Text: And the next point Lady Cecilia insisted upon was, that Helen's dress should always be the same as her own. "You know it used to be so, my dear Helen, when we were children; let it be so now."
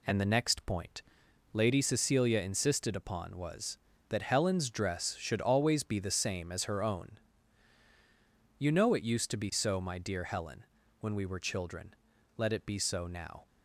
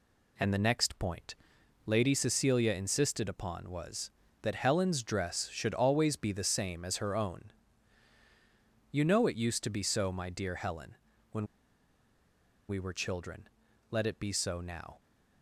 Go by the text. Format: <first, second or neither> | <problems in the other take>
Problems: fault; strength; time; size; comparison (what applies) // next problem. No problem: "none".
first | pauses between "point" and "Lady"; noticeable; at 1.3 s; 0.52 s long; noticeable in the first // pauses between "when" and "we"; at 11.4 s; 1.2 s long